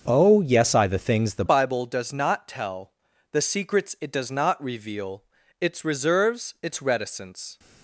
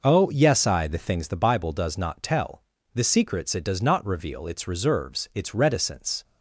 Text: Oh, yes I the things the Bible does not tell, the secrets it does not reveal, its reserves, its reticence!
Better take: second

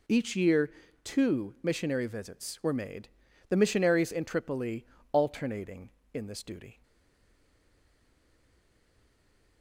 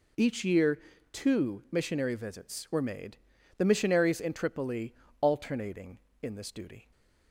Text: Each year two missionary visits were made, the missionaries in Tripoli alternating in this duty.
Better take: second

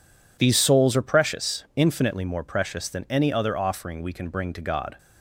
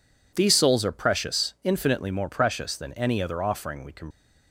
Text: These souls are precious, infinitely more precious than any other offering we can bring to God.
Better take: first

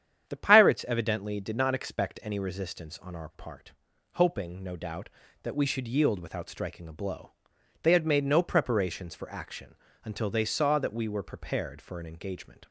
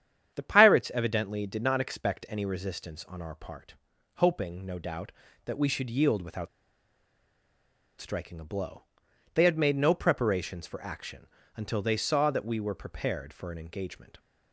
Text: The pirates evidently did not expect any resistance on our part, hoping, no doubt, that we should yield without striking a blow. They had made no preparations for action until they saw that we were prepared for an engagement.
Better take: first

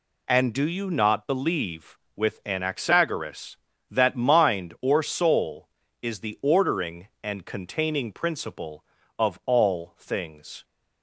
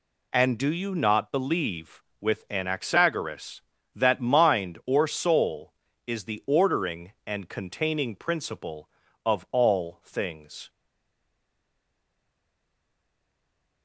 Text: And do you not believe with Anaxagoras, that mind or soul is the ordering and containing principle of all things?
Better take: first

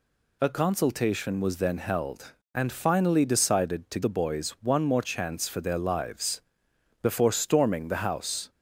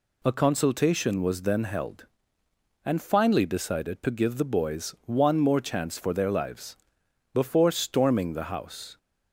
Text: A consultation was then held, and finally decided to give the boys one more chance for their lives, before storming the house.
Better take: second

